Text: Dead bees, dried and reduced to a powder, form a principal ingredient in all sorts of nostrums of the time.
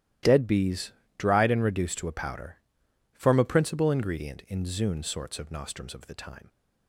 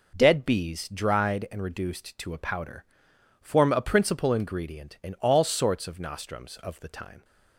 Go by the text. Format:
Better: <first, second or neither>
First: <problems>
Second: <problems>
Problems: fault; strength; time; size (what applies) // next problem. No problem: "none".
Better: second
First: starts louder than the rest; strong; until 1.4 s; 13.5 dB // says "zune" for "all"; at 4.6 s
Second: none